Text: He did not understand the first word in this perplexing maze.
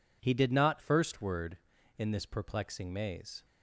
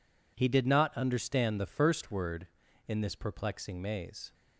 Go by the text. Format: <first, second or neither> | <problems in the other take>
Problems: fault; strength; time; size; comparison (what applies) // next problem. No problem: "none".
second | skips "understand the"; at 0.7 s